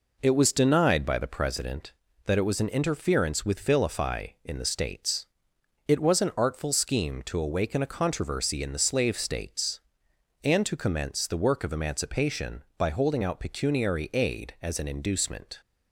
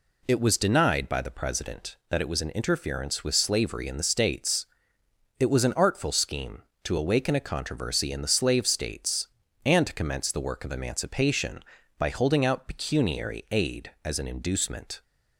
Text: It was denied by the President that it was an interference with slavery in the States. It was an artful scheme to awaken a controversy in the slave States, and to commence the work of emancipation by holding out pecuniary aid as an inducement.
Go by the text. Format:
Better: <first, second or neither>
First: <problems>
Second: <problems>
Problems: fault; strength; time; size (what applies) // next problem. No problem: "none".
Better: second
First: says "vilify" for "slavery"; at 3.6 s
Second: none